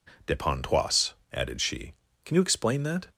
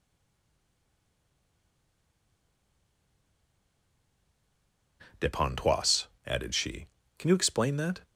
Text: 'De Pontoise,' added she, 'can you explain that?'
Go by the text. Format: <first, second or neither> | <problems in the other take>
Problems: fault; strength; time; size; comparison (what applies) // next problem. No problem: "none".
first | stays silent before the first word; strong; until 5.0 s; 5.0 s long